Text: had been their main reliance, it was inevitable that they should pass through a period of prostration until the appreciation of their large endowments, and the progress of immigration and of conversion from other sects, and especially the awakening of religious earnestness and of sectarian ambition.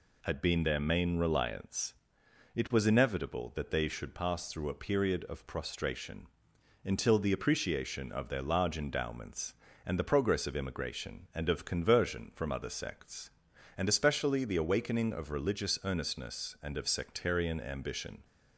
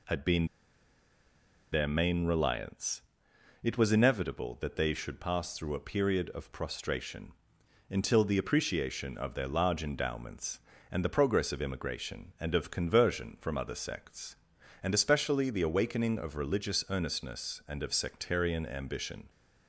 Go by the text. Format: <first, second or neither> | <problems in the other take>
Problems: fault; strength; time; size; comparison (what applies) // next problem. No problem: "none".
first | pauses between "been" and "their"; strong; at 0.4 s; 1.2 s long // pauses between "prostration" and "until"; noticeable; at 7.3 s; 0.58 s long; noticeable in the first